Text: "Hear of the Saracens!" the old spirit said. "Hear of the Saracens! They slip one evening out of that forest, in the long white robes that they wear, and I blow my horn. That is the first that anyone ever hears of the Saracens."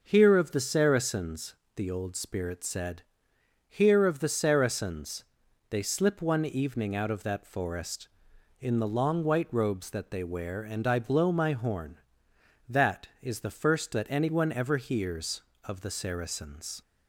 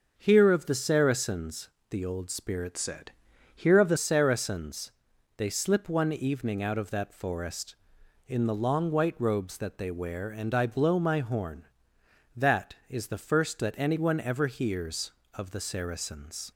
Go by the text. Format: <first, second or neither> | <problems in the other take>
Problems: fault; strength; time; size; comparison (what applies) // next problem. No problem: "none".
first | starts louder than the rest; until 1.1 s; 6.5 dB // changes voice from "said" to "the"; from 2.7 to 3.9 s; 1.2 s long